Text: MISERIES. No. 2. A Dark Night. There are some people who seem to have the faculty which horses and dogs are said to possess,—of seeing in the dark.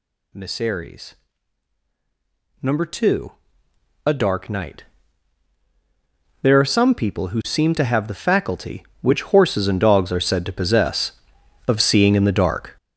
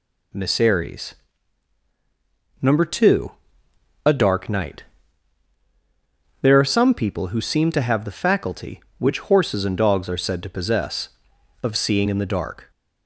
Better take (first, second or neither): second